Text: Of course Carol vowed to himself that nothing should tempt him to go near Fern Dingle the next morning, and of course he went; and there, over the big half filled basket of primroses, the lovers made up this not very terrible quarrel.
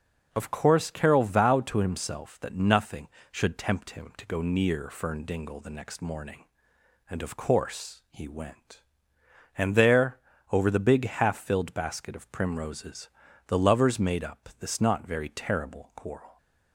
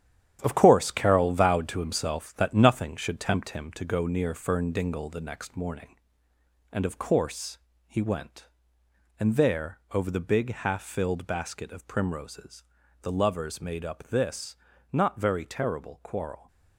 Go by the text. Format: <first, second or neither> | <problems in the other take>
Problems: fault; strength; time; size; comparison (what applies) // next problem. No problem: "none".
first | gets quieter; strong; throughout; 8 dB // pauses between "course" and "he"; slight; at 7.5 s; 0.28 s long // pauses between "this" and "not"; at 14.5 s; 0.38 s long